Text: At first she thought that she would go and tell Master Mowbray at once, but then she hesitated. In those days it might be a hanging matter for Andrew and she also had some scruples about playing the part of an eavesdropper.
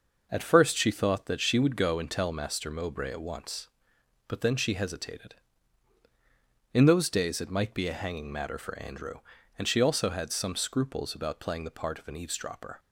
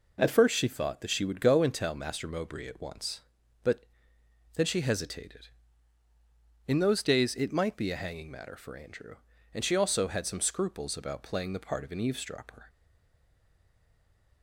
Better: first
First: none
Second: pauses between "but" and "then"; noticeable; at 3.8 s; 0.70 s long // stays silent after the last word; noticeable; from 12.6 s on; 1.8 s long

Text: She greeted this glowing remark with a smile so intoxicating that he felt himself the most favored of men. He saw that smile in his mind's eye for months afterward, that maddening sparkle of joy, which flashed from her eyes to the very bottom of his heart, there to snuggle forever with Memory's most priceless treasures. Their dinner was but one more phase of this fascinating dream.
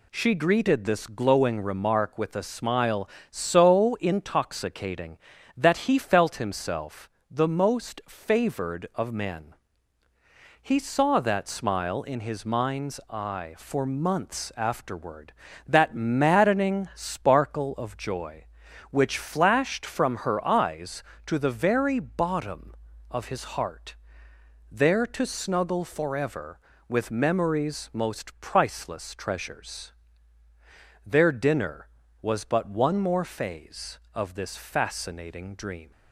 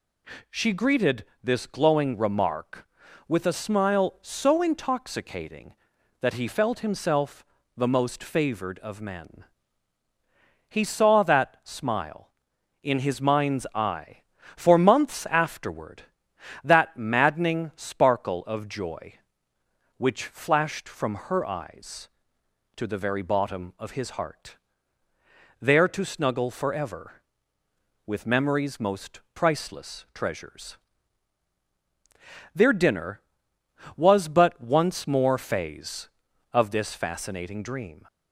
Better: first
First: pauses between "himself" and "the"; slight; at 7.1 s; 0.20 s long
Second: pauses between "greeted" and "this"; slight; at 1.2 s; 0.18 s long // pauses between "himself" and "the"; slight; at 7.4 s; 0.32 s long // says "once" for "one"; at 34.6 s

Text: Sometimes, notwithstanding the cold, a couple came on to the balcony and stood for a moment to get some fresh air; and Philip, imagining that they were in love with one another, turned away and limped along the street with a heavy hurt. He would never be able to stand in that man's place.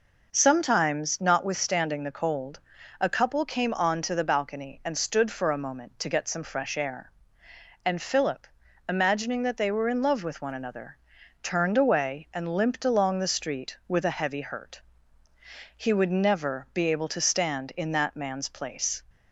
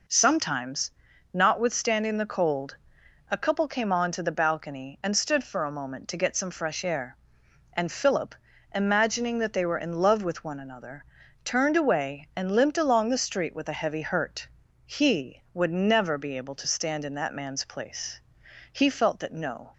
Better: first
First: none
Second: goes on to say "He felt that no"; noticeable; from 18.7 s on; 1.0 s long

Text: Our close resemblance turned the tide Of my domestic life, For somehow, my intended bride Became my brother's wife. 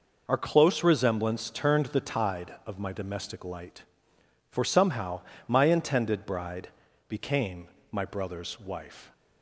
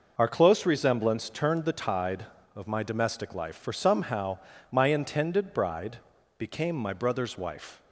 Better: second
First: says "light" for "life"; at 3.4 s // pauses between "bride" and "Became"; at 6.6 s; 0.40 s long // pauses between "Became" and "my"; slight; at 7.6 s; 0.24 s long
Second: pauses between "bride" and "Became"; at 5.9 s; 0.40 s long

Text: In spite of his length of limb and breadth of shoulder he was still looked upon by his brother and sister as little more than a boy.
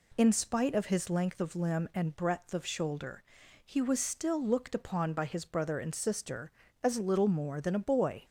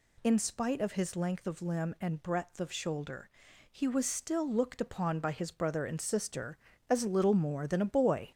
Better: first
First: pauses between "shoulder" and "he"; at 3.2 s; 0.42 s long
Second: gets louder; noticeable; throughout; 4.5 dB // pauses between "shoulder" and "he"; at 3.2 s; 0.42 s long

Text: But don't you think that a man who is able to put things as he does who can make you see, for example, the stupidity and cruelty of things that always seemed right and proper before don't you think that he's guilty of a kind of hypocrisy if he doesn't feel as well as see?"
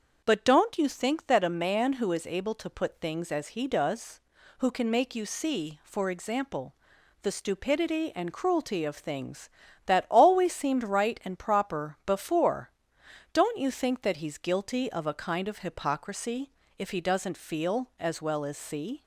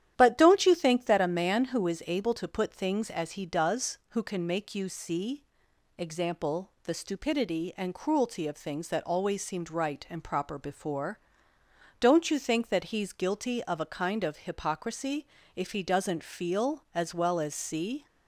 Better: first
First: starts louder than the rest; until 1.2 s; 7 dB // pauses between "before" and "don't"; noticeable; at 12.7 s; 0.62 s long // pauses between "hypocrisy" and "if"; slight; at 16.5 s; 0.28 s long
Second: starts louder than the rest; strong; until 1.1 s; 11 dB // skips "for"; at 5.7 s // pauses between "before" and "don't"; noticeable; at 11.1 s; 0.80 s long // pauses between "hypocrisy" and "if"; slight; at 15.2 s; 0.30 s long

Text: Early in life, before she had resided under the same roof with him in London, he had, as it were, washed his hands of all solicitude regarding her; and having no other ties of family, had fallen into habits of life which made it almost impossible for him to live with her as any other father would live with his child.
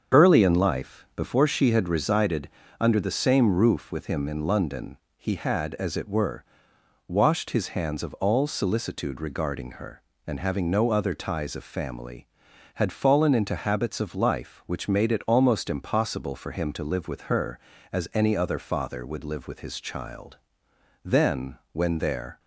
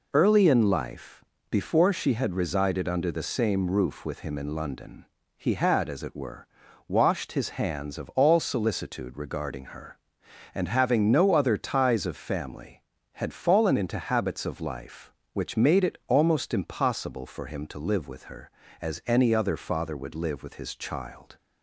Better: second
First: starts louder than the rest; until 1.2 s; 7 dB // pauses between "resided" and "under"; slight; at 2.4 s; 0.32 s long // goes on to say "Then when there"; from 21.0 s on; 1.3 s long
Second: none

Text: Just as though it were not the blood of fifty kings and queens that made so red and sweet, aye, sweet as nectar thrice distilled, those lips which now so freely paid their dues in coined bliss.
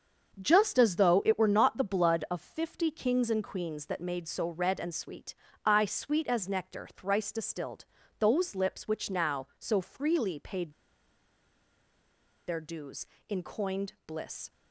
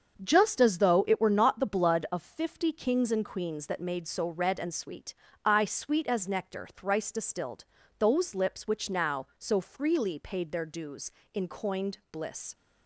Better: second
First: starts louder than the rest; until 1.4 s; 7 dB // pauses between "paid" and "their"; strong; at 10.7 s; 1.7 s long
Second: starts louder than the rest; until 1.2 s; 7 dB

